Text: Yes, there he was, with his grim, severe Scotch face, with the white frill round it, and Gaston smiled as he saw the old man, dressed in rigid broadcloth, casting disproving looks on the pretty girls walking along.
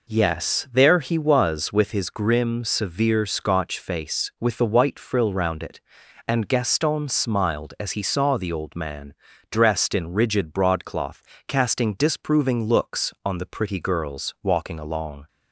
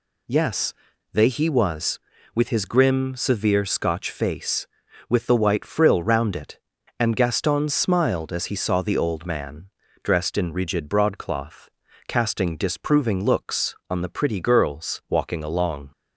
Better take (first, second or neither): first